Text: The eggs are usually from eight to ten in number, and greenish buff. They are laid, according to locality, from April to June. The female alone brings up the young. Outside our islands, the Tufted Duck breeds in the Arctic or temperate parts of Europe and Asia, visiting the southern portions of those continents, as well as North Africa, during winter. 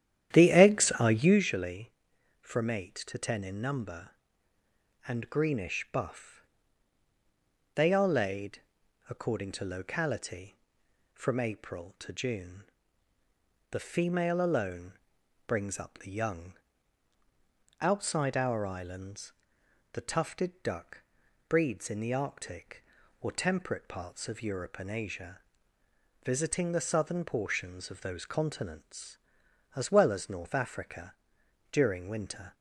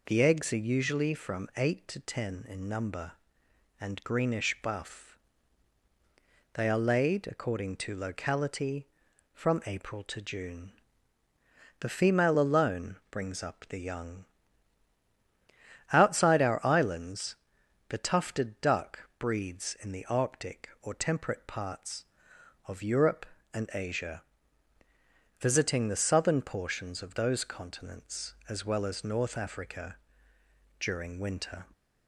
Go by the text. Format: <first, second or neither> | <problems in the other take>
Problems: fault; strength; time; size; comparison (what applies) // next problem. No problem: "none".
second | starts louder than the rest; strong; until 1.6 s; 10.5 dB // pauses between "alone" and "brings"; noticeable; at 14.9 s; 0.56 s long // pauses between "Duck" and "breeds"; noticeable; at 21.0 s; 0.46 s long